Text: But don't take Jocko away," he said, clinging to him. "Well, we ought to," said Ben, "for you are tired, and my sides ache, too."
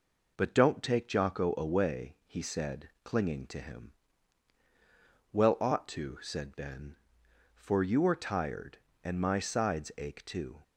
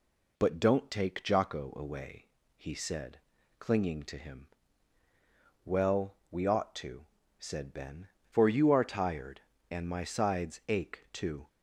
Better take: second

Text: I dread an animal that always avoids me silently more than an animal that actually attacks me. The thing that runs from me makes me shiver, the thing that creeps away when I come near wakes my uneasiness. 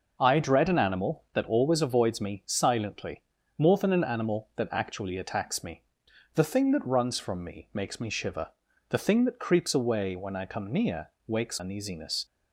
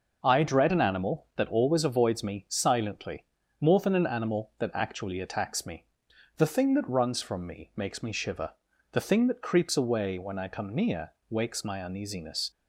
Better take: second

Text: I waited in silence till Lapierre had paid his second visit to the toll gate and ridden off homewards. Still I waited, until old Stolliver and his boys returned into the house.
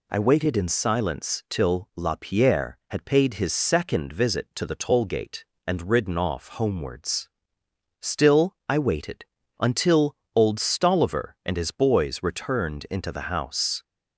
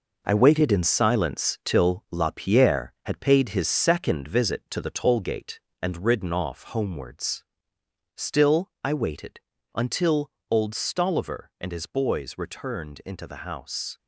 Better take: first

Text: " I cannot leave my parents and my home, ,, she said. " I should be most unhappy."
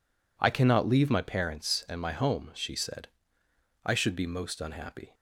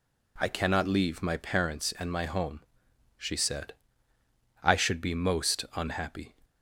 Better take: neither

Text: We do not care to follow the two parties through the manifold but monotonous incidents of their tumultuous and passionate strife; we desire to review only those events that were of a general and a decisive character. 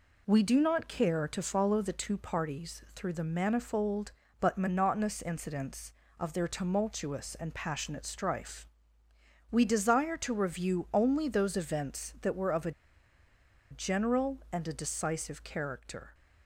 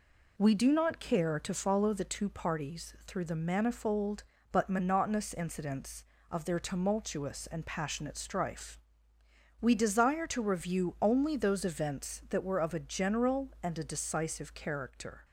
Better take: second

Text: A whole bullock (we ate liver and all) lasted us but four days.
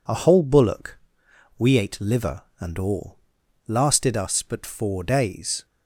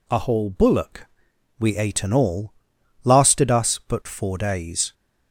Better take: first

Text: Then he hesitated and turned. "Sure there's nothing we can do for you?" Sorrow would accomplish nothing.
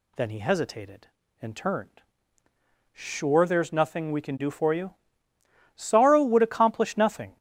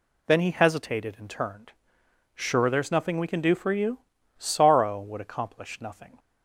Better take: neither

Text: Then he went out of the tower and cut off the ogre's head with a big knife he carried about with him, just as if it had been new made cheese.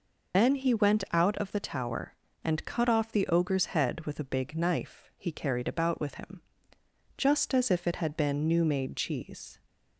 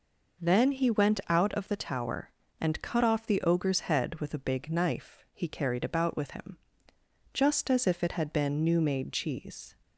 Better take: second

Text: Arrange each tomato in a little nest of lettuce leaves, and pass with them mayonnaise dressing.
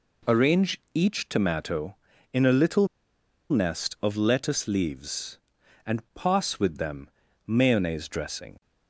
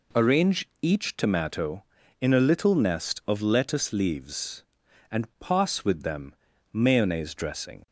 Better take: second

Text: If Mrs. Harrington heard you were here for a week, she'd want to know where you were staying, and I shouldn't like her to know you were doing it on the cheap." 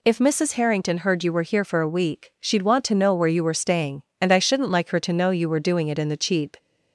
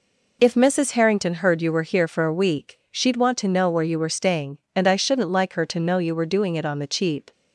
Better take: second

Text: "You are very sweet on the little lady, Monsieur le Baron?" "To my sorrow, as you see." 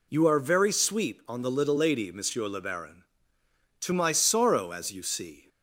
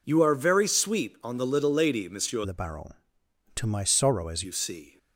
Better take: first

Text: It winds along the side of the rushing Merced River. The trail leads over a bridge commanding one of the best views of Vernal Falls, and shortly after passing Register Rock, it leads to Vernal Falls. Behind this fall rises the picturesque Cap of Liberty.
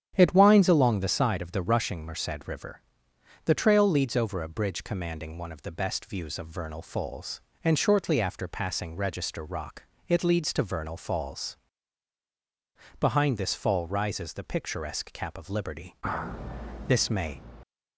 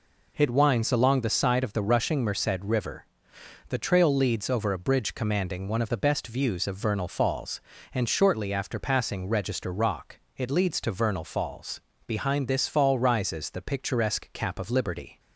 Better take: second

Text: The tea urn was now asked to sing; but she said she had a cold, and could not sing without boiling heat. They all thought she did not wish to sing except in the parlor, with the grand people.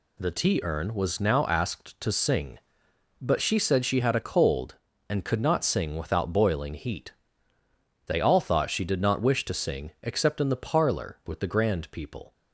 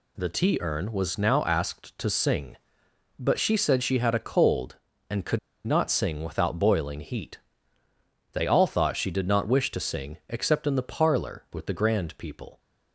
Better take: first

